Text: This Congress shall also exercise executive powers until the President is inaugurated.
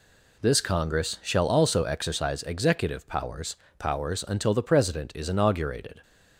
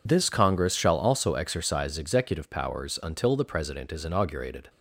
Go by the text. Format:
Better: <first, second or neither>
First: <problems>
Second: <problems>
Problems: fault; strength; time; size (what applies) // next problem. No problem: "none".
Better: second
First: says "powers" twice; at 3.7 s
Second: none